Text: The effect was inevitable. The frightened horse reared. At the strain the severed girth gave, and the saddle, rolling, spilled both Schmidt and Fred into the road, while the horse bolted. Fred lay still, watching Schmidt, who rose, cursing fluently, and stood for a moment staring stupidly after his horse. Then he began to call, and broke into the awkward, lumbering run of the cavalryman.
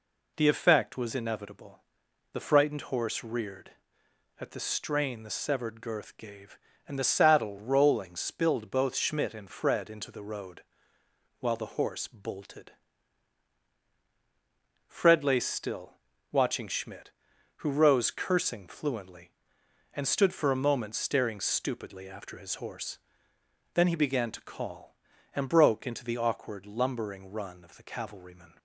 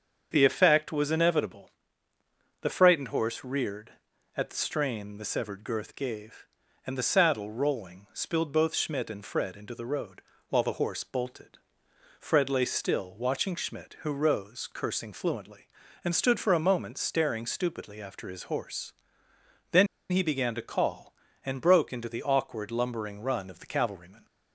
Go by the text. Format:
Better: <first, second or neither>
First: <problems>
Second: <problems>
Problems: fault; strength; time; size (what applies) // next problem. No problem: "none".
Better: first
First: none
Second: starts louder than the rest; strong; until 1.3 s; 7 dB // pauses between "Then" and "he"; slight; at 19.8 s; 0.25 s long